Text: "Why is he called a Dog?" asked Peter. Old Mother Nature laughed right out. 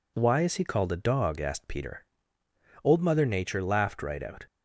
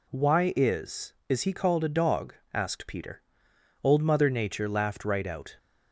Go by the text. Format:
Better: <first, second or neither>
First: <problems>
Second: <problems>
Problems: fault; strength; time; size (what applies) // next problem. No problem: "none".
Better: first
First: none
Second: says "is" twice; at 1.2 s